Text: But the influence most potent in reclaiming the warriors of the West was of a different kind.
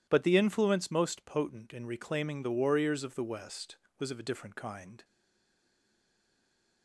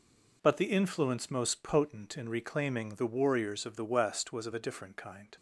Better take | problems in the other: second | stays silent after the last word; noticeable; from 5.0 s on; 1.8 s long

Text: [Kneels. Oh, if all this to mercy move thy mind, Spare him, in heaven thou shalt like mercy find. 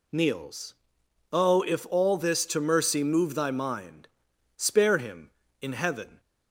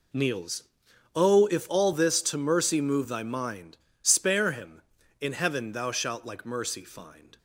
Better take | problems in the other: second | stops before "thou shalt like mercy find"; at 6.1 s

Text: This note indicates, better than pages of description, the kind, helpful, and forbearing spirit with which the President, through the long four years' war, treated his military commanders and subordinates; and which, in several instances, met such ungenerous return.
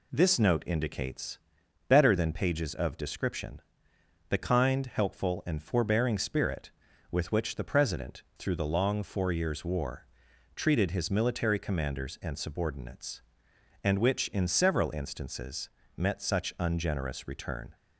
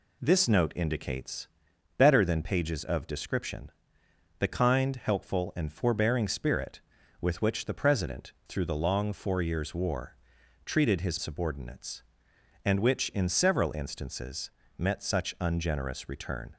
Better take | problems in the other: first | skips "military commanders and"; at 11.1 s

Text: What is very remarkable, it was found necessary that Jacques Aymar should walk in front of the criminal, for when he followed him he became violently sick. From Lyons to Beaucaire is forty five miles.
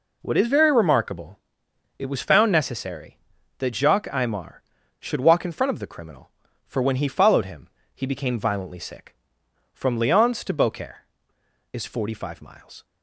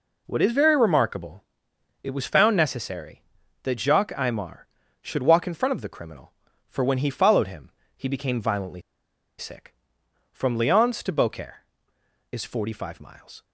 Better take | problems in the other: first | pauses between "him" and "he"; slight; at 7.6 s; 0.26 s long; slight in the first // pauses between "violently" and "sick"; noticeable; at 8.8 s; 0.57 s long

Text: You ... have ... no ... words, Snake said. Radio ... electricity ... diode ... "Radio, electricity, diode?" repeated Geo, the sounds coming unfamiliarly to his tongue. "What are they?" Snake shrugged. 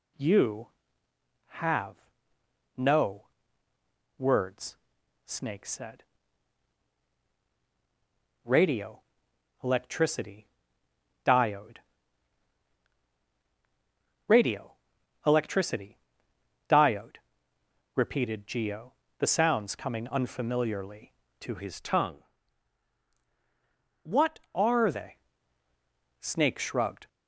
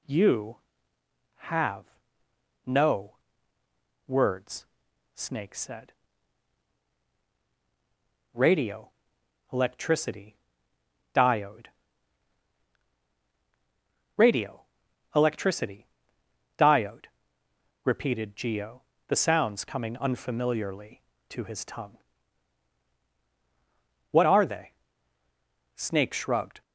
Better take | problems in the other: second | changes voice from "his" to "are"; from 21.5 to 24.9 s; 3.4 s long

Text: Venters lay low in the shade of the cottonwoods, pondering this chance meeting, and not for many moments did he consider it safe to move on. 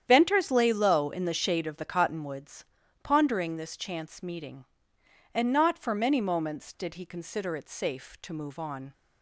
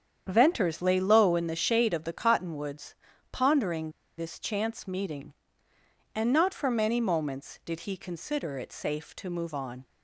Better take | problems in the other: first | starts louder than the rest; strong; until 1.2 s; 8.5 dB; strong in the first // pauses between "pondering" and "this"; slight; at 3.9 s; 0.26 s long

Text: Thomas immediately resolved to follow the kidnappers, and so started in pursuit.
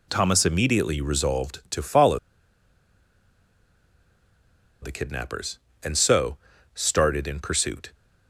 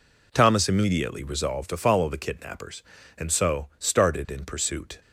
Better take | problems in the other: second | pauses between "follow" and "the"; strong; at 2.1 s; 2.6 s long // pauses between "so" and "started"; slight; at 6.3 s; 0.36 s long

